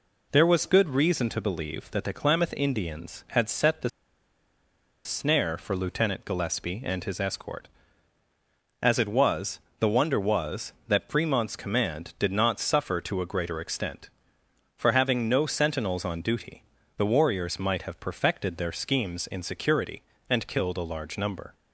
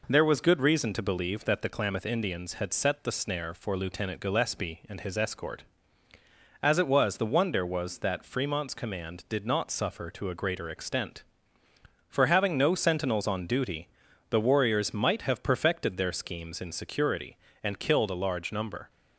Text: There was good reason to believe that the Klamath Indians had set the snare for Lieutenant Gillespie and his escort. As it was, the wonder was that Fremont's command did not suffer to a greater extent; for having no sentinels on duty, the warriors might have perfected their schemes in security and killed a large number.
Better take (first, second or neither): second